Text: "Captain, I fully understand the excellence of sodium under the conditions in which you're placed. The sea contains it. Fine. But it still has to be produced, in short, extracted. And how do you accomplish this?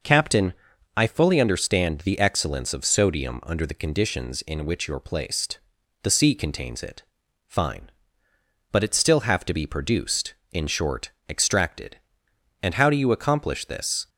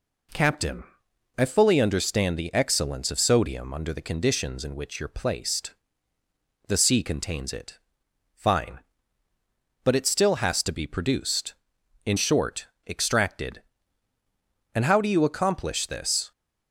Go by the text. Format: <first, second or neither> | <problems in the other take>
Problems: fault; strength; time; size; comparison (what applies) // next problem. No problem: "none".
second | says "have" for "has"; at 9.2 s